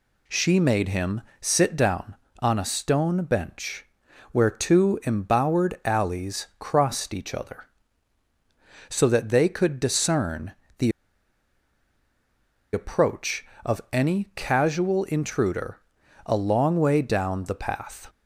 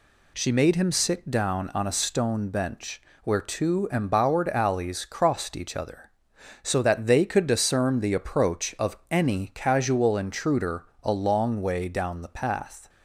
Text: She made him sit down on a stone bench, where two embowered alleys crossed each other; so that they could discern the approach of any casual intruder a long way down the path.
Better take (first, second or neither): second